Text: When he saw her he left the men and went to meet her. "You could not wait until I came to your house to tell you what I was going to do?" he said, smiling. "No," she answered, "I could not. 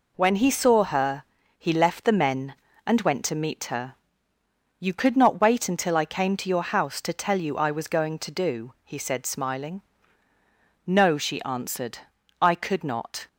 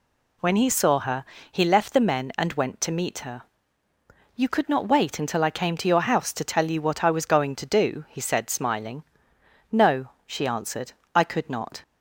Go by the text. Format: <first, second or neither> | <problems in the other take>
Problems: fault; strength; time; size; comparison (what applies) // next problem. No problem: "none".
second | pauses between "her" and "he"; slight; at 1.2 s; 0.34 s long; slight in the second // skips "what"; at 7.5 s